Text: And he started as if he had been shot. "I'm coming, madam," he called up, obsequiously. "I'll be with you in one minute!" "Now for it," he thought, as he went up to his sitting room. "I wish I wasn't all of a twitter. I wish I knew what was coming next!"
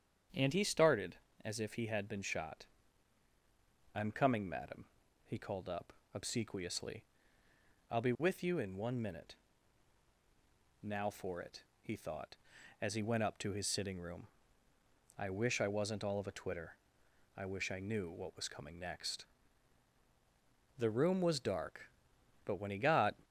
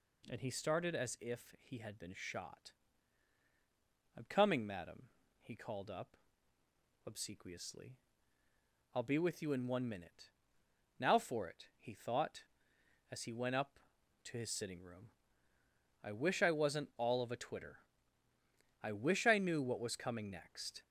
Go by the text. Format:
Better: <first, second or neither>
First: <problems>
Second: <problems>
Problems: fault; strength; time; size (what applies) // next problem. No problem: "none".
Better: second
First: starts louder than the rest; strong; until 1.6 s; 7.5 dB // goes on to say "The room was dark but when he got"; strong; from 20.7 s on; 2.3 s long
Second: none